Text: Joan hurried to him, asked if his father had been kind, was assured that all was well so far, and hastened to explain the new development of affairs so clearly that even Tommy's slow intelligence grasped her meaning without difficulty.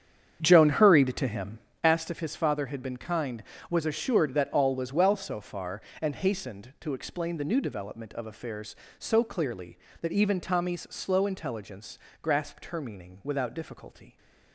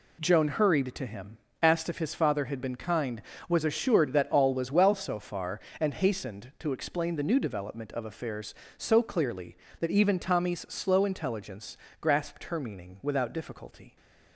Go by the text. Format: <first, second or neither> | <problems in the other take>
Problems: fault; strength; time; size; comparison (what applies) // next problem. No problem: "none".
second | starts louder than the rest; strong; until 1.9 s; 8 dB // pauses between "intelligence" and "grasped"; slight; at 11.9 s; 0.24 s long; slight in the second